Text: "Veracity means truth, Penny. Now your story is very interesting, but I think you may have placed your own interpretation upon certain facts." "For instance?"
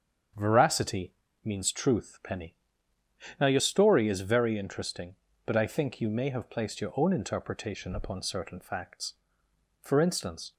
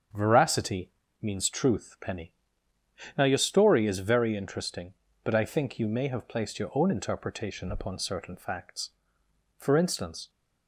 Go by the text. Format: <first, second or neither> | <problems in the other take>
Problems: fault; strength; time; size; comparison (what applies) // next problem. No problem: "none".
neither | starts louder than the rest; strong; the same in both // pauses between "Veracity" and "means"; slight; the same in both